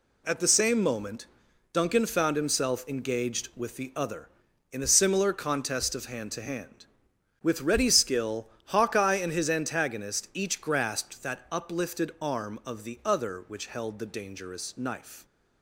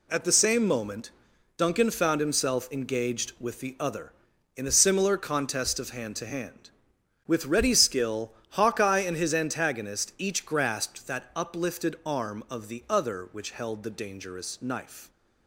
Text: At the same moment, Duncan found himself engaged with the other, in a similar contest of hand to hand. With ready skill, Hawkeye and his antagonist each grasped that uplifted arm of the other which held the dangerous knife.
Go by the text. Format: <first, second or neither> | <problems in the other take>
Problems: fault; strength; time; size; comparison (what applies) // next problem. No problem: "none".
neither | none